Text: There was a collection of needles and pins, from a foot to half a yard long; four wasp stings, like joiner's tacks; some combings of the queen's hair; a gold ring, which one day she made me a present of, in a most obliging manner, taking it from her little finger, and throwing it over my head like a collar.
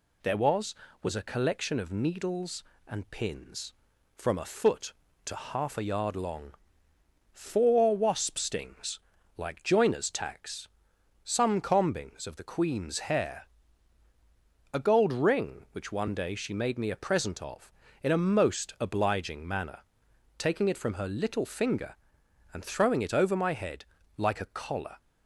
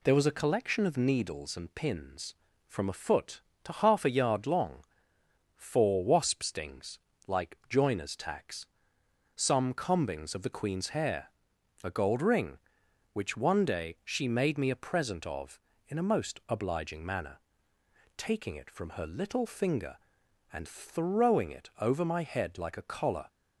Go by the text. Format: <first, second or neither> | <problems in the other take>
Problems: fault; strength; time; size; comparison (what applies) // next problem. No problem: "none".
second | says "was" twice; at 1.0 s // pauses between "head" and "like"; slight; at 23.8 s; 0.32 s long